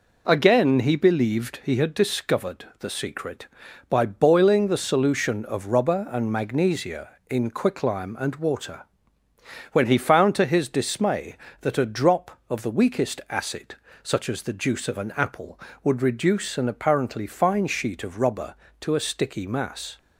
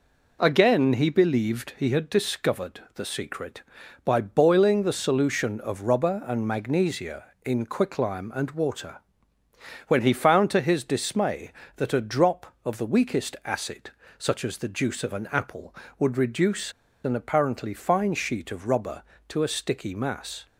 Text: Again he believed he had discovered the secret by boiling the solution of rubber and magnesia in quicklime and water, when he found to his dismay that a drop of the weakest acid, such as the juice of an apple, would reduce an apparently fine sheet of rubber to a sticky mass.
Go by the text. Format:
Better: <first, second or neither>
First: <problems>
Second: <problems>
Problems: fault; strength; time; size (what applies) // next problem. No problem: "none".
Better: first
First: none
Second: pauses between "reduce" and "an"; slight; at 16.7 s; 0.32 s long